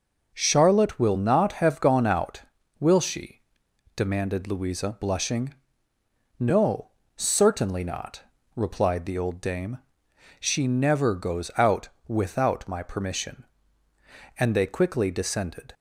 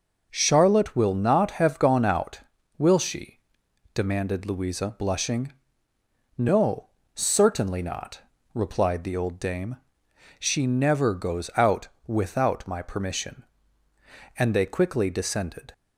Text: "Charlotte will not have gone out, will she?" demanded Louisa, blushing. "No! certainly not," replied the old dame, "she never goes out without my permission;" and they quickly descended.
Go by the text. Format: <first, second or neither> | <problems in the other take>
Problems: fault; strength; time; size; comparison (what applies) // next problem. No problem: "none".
neither | pauses between "out" and "without"; slight; the same in both